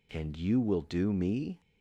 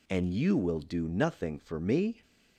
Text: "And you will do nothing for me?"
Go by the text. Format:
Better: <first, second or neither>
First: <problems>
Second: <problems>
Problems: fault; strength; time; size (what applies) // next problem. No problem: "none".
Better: second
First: skips "nothing for"; at 1.1 s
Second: none